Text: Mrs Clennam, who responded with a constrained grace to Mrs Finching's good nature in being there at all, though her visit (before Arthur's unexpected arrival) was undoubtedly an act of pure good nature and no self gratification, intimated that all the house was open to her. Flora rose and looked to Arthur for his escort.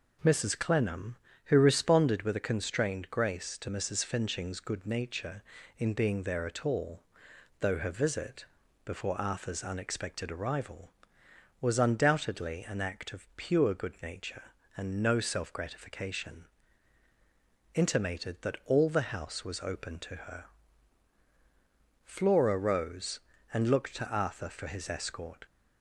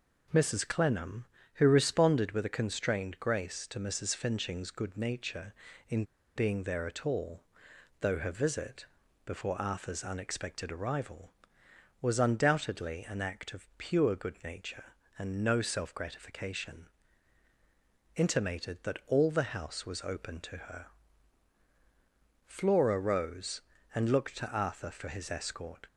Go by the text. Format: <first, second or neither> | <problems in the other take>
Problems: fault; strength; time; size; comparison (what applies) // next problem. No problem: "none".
first | pauses between "in" and "being"; slight; at 6.0 s; 0.32 s long